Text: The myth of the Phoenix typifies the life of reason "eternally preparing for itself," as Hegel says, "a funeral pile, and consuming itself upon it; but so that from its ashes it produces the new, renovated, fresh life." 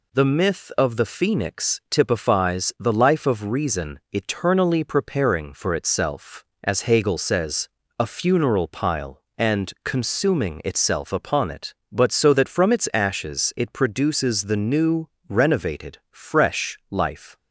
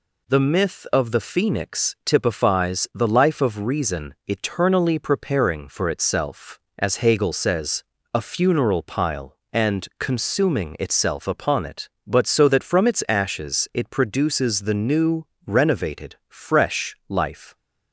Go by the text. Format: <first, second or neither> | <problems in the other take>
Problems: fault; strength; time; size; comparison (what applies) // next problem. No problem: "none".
neither | none